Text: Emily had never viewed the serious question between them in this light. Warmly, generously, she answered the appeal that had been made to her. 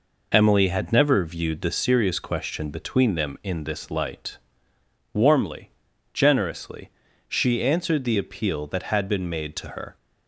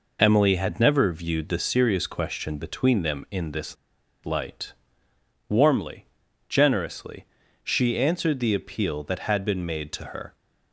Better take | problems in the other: first | pauses between "this" and "light"; noticeable; at 3.7 s; 0.50 s long

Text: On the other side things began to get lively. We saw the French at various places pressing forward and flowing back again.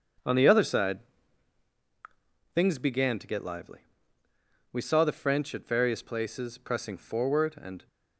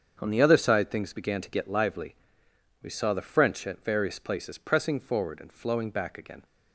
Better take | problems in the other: second | starts louder than the rest; until 2.8 s; 6.5 dB; also in the second // pauses between "side" and "things"; strong; at 0.9 s; 1.5 s long // stops before "flowing back again"; at 7.8 s

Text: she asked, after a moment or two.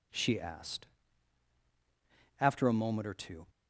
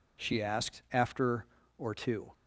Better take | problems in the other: first | skips "a moment"; at 1.6 s

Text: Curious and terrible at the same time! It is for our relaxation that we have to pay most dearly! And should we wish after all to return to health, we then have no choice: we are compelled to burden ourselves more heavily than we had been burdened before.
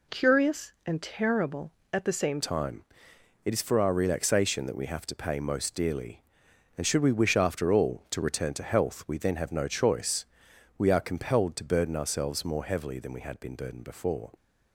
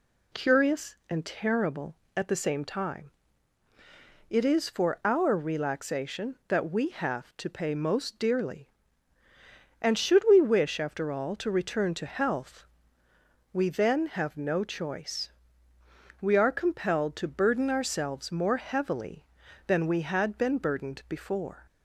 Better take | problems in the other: second | changes voice at "time"; from 2.4 s on; 11.9 s long

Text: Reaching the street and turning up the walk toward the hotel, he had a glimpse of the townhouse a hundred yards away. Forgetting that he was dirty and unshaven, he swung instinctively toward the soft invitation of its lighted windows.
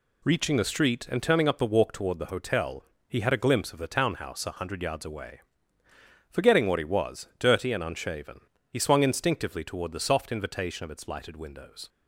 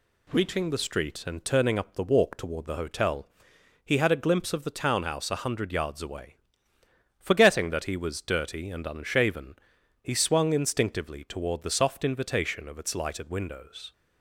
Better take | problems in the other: second | says "what" for "that"; at 6.6 s

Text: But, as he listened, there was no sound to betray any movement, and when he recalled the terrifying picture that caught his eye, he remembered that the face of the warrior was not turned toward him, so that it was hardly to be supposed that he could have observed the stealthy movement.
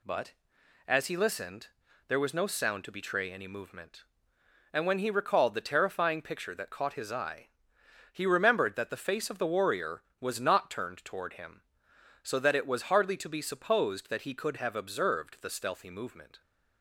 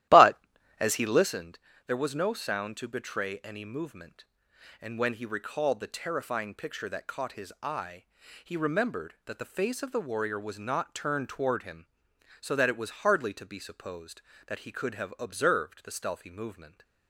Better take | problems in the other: first | starts louder than the rest; strong; until 1.4 s; 14 dB

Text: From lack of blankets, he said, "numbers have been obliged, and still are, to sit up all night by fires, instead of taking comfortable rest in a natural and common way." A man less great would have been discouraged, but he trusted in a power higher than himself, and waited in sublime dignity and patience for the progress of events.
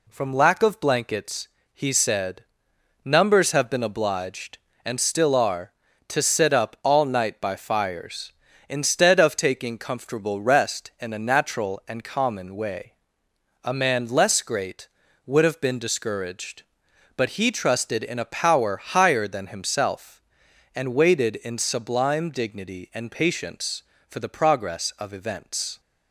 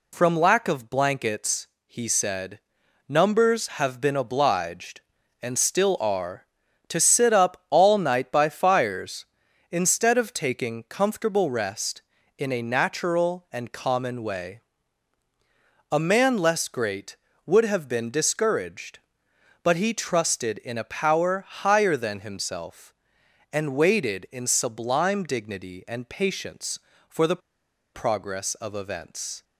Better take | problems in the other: first | pauses between "the" and "progress"; noticeable; at 27.4 s; 0.54 s long

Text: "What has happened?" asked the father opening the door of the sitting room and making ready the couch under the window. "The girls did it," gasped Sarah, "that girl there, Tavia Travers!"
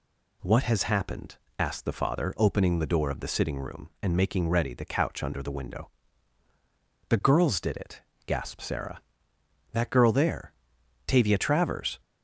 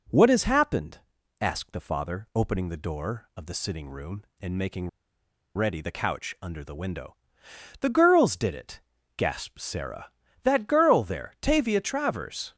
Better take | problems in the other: first | pauses between "making" and "ready"; noticeable; at 4.8 s; 0.67 s long

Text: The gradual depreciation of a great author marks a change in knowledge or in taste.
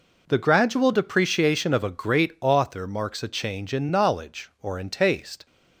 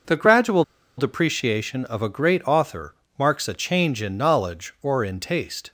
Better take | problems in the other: first | pauses between "gradual" and "depreciation"; slight; at 0.6 s; 0.35 s long // pauses between "author" and "marks"; slight; at 2.9 s; 0.22 s long

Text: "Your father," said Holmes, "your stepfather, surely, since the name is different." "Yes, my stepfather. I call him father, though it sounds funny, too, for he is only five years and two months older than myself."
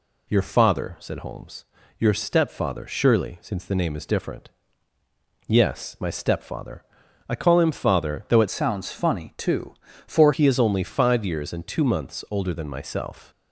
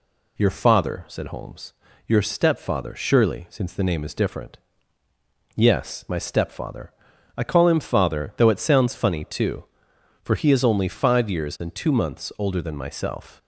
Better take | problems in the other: second | changes voice from "sounds" to "for"; from 8.5 to 10.3 s; 1.8 s long

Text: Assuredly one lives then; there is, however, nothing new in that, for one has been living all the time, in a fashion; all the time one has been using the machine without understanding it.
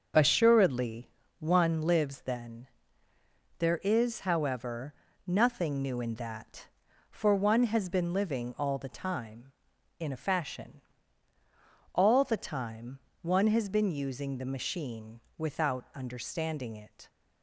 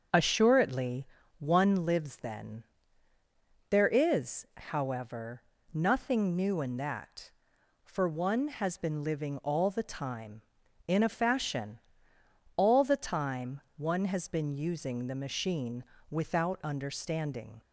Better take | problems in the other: first | starts louder than the rest; until 1.4 s; 7 dB; also in the first // pauses between "Assuredly" and "one"; slight; at 1.0 s; 0.32 s long; slight in the first // pauses between "time" and "one"; slight; at 13.6 s; 0.16 s long; slight in the first // pauses between "machine" and "without"; slight; at 15.8 s; 0.26 s long; slight in the first // stops before "it"; at 17.6 s

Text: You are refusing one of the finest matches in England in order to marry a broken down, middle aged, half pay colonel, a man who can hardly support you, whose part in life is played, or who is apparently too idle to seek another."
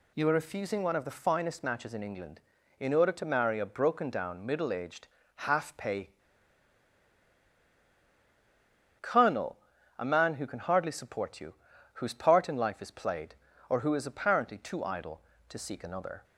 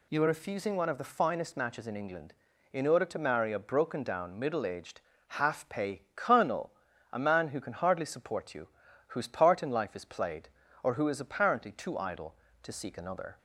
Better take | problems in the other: second | pauses between "pay" and "colonel"; strong; at 6.0 s; 2.9 s long

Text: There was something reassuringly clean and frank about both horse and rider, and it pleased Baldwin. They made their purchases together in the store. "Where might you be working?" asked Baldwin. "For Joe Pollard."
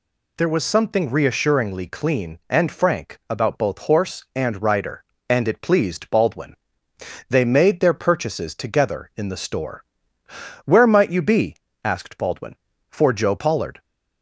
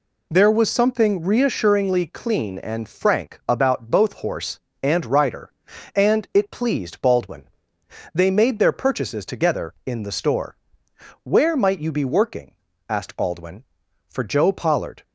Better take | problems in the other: second | skips "working"; at 11.6 s

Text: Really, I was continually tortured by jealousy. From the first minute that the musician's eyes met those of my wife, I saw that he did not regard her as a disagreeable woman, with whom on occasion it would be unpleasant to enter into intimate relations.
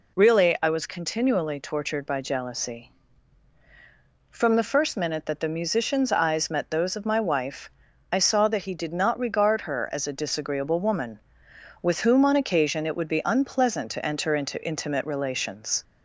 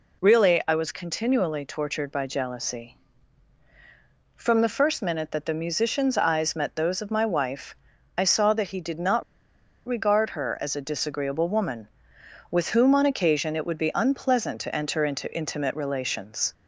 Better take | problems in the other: first | pauses between "not" and "regard"; noticeable; at 9.2 s; 0.63 s long

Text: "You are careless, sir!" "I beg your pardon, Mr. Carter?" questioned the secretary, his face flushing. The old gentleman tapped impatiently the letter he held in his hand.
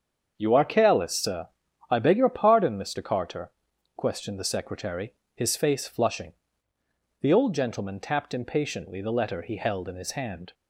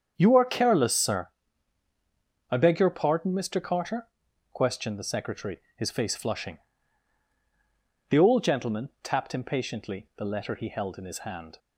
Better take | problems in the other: neither | starts louder than the rest; strong; the same in both

